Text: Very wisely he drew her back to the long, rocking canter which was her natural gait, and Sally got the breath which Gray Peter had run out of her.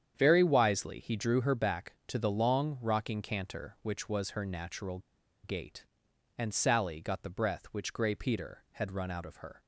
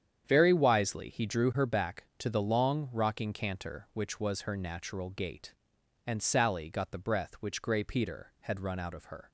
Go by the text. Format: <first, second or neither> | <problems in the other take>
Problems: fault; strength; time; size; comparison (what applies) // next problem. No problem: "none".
second | starts louder than the rest; strong; until 1.1 s; 8.5 dB; strong in the second // pauses between "natural" and "gait"; at 4.9 s; 0.44 s long